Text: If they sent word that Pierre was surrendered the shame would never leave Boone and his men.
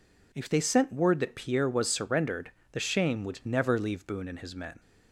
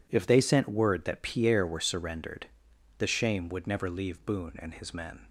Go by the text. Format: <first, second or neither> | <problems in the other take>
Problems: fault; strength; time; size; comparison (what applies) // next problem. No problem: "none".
first | says "were" for "was"; at 1.6 s // pauses between "surrendered" and "the"; noticeable; at 2.4 s; 0.50 s long; slight in the first